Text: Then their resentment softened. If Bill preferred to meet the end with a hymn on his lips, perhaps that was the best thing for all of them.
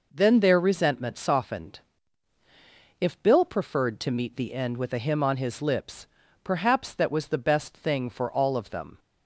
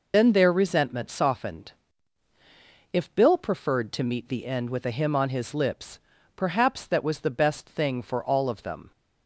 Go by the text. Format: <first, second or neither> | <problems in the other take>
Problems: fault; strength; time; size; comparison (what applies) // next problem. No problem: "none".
first | loses the start of "Then"; at 0.1 s; 100 ms